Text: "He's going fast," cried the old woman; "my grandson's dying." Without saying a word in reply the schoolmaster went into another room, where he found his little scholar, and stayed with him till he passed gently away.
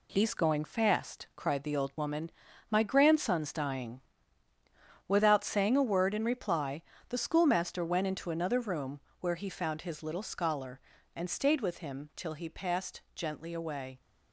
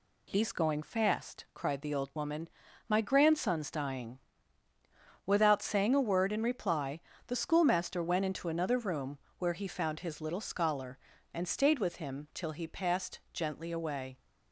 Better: second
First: gets quieter; noticeable; throughout; 6 dB // pauses between "reply" and "the"; slight; at 6.8 s; 0.28 s long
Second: pauses between "reply" and "the"; slight; at 7.0 s; 0.28 s long

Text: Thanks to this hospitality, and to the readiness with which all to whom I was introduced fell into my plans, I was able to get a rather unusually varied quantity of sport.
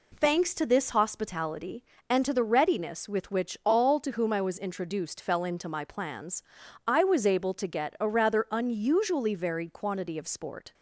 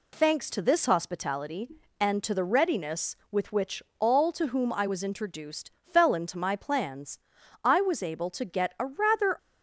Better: first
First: none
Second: pauses between "which" and "all"; slight; at 3.8 s; 0.16 s long // pauses between "introduced" and "fell"; slight; at 5.7 s; 0.20 s long // stops before "unusually varied quantity of sport"; at 9.3 s

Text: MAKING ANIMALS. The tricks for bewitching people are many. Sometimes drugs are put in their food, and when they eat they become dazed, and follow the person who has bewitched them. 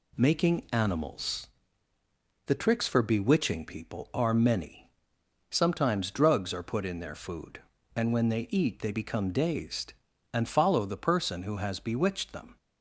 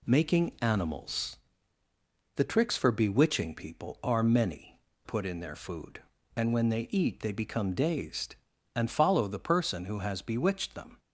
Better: first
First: none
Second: skips "Sometimes drugs are"; at 4.9 s

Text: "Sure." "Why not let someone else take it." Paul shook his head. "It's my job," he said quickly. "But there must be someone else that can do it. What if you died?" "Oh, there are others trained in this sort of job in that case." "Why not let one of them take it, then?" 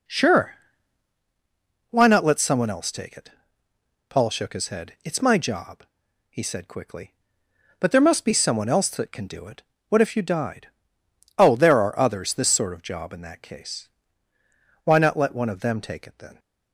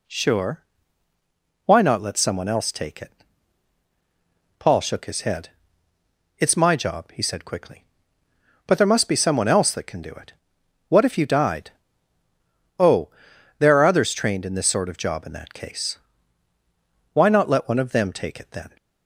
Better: second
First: skips "trained in"; at 12.3 s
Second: none

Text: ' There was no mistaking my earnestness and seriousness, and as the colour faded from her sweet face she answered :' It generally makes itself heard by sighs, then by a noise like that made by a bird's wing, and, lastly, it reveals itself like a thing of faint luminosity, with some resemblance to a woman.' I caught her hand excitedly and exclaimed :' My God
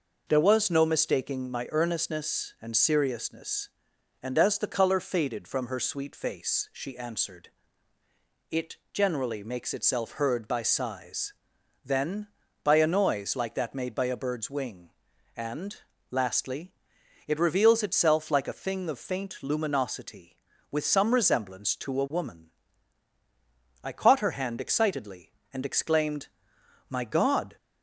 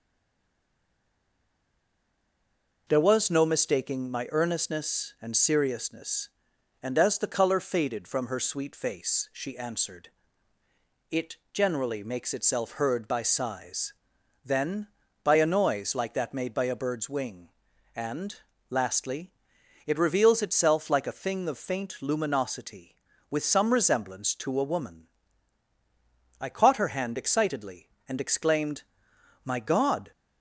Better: first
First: pauses between "It" and "generally"; slight; at 8.7 s; 0.16 s long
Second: stays silent before the first word; strong; until 2.8 s; 2.8 s long // pauses between "It" and "generally"; slight; at 11.3 s; 0.16 s long

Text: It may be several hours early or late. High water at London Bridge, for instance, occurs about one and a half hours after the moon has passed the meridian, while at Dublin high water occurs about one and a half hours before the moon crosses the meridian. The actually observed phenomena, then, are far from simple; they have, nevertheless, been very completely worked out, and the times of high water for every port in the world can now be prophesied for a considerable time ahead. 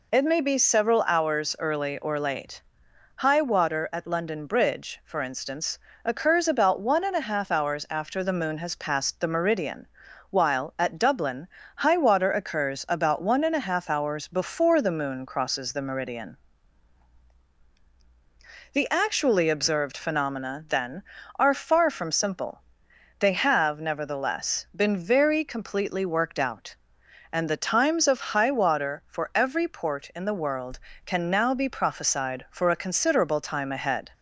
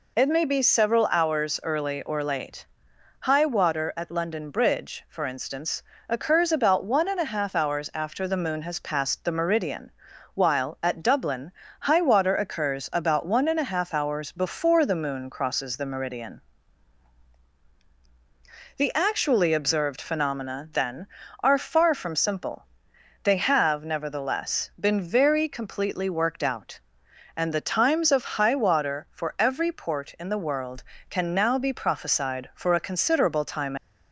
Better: first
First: pauses between "Dublin" and "high"; slight; at 11.4 s; 0.30 s long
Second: pauses between "Dublin" and "high"; slight; at 11.4 s; 0.30 s long // stops before "ahead"; at 33.7 s

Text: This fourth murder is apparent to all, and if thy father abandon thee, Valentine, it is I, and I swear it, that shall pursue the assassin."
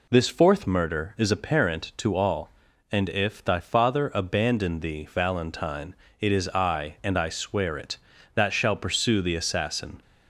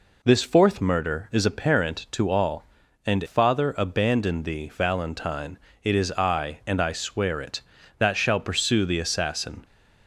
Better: first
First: none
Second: skips "if thy"; at 3.2 s

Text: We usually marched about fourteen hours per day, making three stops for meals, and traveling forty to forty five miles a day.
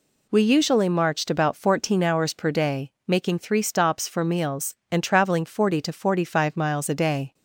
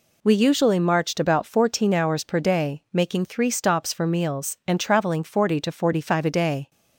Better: first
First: none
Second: skips "miles"; at 6.2 s

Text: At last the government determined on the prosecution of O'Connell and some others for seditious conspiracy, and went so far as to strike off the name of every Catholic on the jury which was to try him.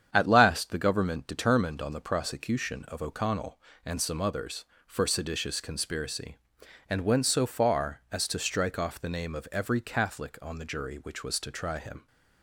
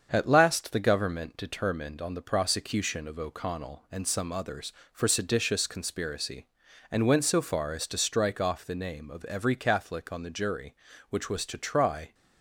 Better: first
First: starts louder than the rest; strong; until 1.1 s; 8.5 dB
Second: starts louder than the rest; strong; until 1.1 s; 7 dB // stops before "him"; at 12.1 s

